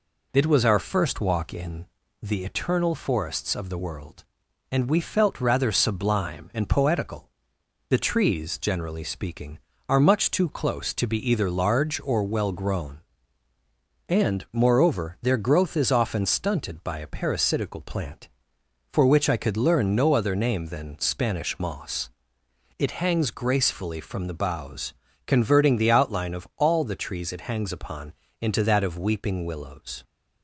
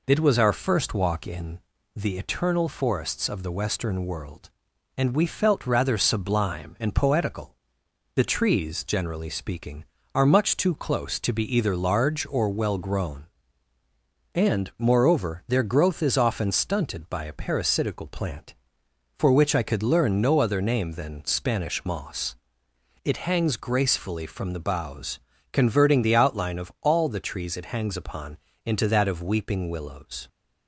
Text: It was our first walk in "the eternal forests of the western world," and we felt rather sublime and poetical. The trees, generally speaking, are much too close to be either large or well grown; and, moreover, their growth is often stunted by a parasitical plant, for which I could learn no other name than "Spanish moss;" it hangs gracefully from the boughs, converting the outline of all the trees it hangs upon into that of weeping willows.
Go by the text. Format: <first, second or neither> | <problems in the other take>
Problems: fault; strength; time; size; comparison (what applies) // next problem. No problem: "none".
second | pauses between "in" and "the"; slight; at 1.8 s; 0.36 s long; slight in the second // skips "western"; at 3.7 s // pauses between "upon" and "into"; slight; at 28.1 s; 0.26 s long; slight in the second